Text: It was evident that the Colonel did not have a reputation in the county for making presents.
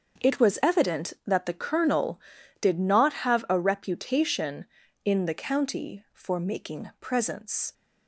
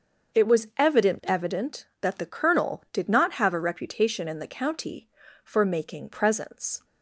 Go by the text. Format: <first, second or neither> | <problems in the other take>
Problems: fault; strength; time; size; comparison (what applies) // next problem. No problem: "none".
first | starts louder than the rest; until 1.5 s; 6.5 dB; also in the first // says "evident" twice; at 1.2 s